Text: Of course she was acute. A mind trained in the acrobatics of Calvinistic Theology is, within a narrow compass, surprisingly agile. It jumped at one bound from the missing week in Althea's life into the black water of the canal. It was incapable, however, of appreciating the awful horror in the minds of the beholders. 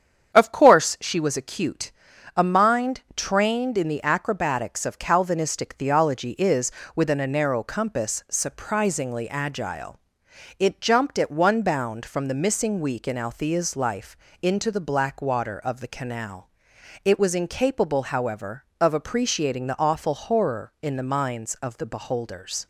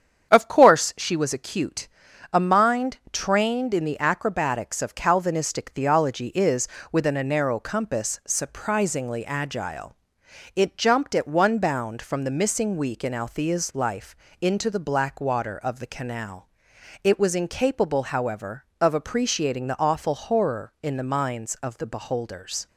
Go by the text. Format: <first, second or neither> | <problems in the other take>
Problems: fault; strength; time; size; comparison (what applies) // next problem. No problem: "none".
neither | starts louder than the rest; strong; the same in both // pauses between "life" and "into"; slight; the same in both